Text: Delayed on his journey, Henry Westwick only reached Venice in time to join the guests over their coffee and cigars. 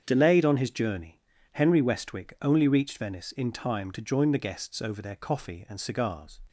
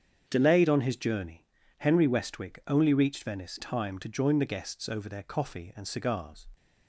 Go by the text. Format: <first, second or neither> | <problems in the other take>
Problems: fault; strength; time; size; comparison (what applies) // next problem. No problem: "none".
first | starts louder than the rest; strong; until 1.2 s; 7.5 dB; strong in the first // skips "in"; at 3.5 s